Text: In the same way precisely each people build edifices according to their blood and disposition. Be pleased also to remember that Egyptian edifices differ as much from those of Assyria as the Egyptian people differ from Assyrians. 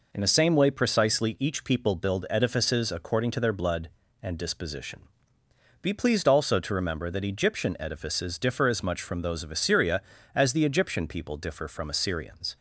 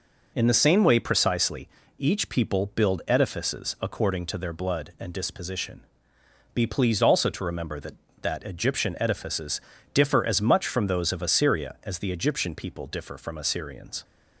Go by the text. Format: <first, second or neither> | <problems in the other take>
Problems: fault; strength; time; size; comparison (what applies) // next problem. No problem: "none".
first | pauses between "precisely" and "each"; slight; at 1.6 s; 0.30 s long // says "that" twice; at 8.2 s // pauses between "edifices" and "differ"; slight; at 9.6 s; 0.32 s long